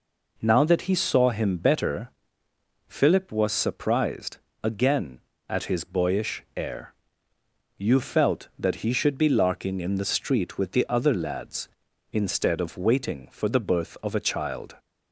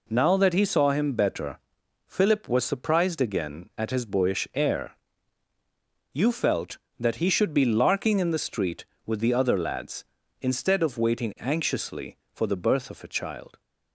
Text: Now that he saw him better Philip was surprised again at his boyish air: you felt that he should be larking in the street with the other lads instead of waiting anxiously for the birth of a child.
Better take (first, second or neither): second